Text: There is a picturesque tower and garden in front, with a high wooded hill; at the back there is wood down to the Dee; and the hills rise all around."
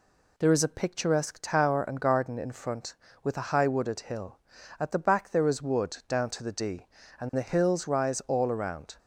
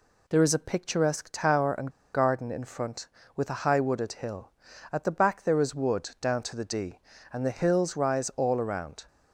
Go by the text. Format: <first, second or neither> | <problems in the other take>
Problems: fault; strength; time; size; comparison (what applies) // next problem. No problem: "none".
first | pauses between "and" and "garden"; slight; at 1.8 s; 0.25 s long